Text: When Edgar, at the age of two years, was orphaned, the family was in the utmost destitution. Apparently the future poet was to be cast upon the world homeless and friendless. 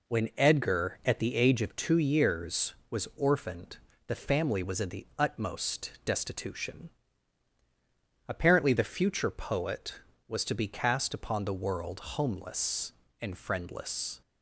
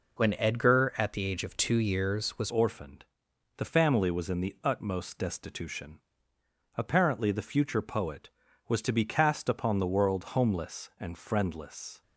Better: first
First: none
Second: changes voice at "orphaned"; from 2.4 s on; 9.6 s long

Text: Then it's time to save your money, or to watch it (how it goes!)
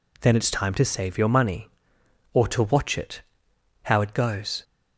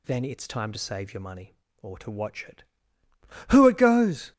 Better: first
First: none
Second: says "who" for "how"; at 3.5 s

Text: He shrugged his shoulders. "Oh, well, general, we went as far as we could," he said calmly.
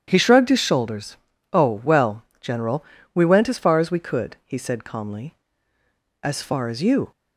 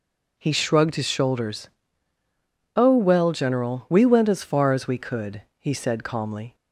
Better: second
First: starts louder than the rest; strong; until 1.0 s; 9.5 dB // goes on to say "As far as you"; noticeable; from 6.2 s on; 0.88 s long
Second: none

